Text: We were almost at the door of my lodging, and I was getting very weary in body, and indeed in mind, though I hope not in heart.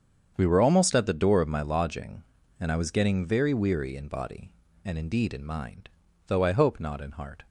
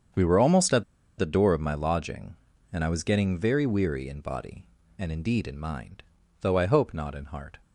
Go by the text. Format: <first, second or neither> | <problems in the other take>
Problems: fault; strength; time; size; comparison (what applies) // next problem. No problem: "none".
first | starts louder than the rest; strong; until 1.5 s; 7.5 dB; strong in the first // pauses between "at" and "the"; slight; at 0.8 s; 0.34 s long